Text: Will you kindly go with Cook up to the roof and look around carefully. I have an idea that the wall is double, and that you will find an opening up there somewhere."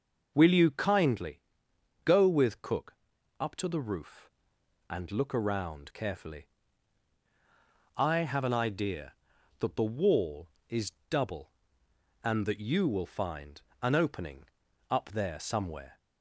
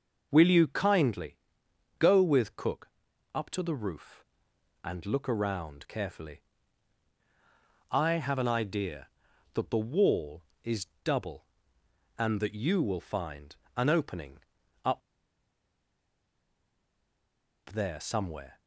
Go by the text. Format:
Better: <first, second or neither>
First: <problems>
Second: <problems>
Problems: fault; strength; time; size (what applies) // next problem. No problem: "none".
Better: first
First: pauses between "kindly" and "go"; noticeable; at 1.4 s; 0.64 s long // pauses between "Cook" and "up"; at 2.9 s; 0.44 s long // pauses between "is" and "double"; slight; at 10.9 s; 0.16 s long // pauses between "find" and "an"; slight; at 13.5 s; 0.22 s long // pauses between "opening" and "up"; at 14.4 s; 0.44 s long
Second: pauses between "kindly" and "go"; noticeable; at 1.3 s; 0.62 s long // pauses between "Cook" and "up"; at 2.8 s; 0.44 s long // pauses between "is" and "double"; slight; at 10.8 s; 0.16 s long // pauses between "find" and "an"; slight; at 13.5 s; 0.22 s long // pauses between "opening" and "up"; at 14.3 s; 0.44 s long // pauses between "up" and "there"; strong; at 15.0 s; 2.7 s long